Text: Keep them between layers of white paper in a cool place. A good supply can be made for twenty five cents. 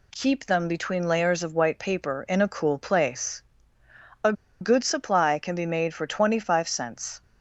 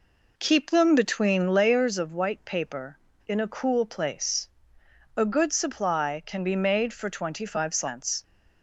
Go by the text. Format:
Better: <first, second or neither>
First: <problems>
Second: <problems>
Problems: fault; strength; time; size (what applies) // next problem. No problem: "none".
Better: second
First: pauses between "A" and "good"; slight; at 4.3 s; 0.28 s long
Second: none